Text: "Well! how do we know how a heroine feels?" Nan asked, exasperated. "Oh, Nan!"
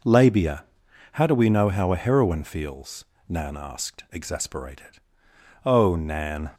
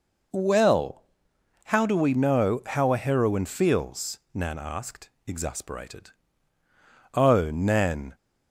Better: second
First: says "Labia" for "Well"; at 0.0 s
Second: none

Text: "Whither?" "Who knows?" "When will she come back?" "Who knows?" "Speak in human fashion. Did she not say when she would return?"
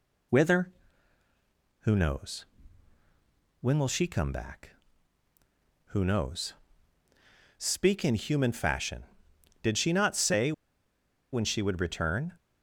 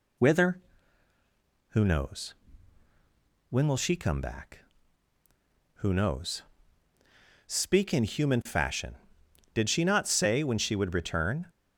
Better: second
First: pauses between "say" and "when"; noticeable; at 10.5 s; 0.81 s long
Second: none

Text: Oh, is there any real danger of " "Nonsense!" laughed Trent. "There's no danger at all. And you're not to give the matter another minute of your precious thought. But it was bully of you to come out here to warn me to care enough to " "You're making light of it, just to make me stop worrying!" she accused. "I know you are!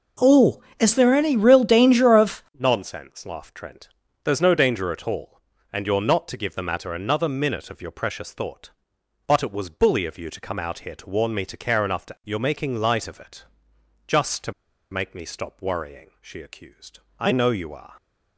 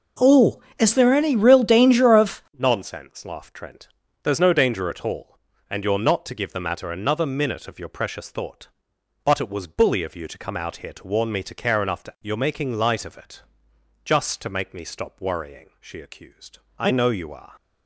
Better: second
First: pauses between "to" and "make"; at 14.5 s; 0.39 s long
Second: none

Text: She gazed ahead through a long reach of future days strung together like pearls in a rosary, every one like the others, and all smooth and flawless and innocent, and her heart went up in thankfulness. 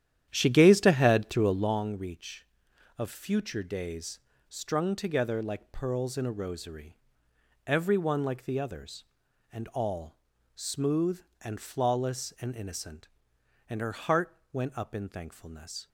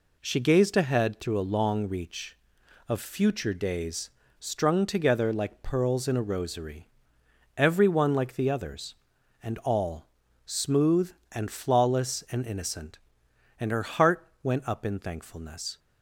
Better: second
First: starts louder than the rest; strong; until 1.8 s; 10.5 dB // pauses between "days" and "strung"; slight; at 4.1 s; 0.28 s long // pauses between "all" and "smooth"; at 10.1 s; 0.38 s long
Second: pauses between "days" and "strung"; slight; at 4.1 s; 0.28 s long // pauses between "all" and "smooth"; at 10.0 s; 0.38 s long

